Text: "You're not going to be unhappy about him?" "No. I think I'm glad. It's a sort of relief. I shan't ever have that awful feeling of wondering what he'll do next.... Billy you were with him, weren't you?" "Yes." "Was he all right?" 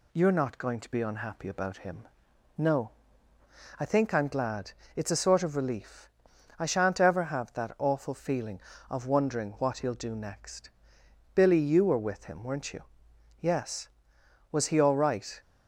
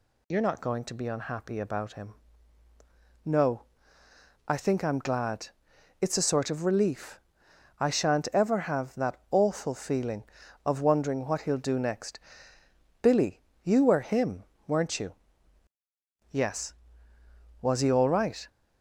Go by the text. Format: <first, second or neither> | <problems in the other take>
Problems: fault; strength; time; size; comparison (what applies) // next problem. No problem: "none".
first | pauses between "Billy" and "you"; slight; at 13.4 s; 0.22 s long // skips "with"; at 14.0 s